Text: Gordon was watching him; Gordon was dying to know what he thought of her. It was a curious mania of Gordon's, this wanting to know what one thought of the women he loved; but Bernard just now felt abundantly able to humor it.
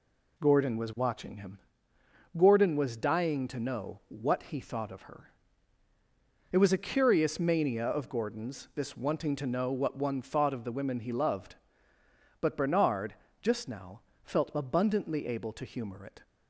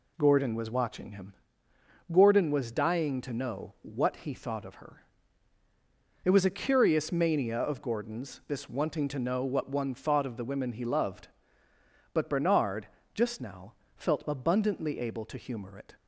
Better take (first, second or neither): neither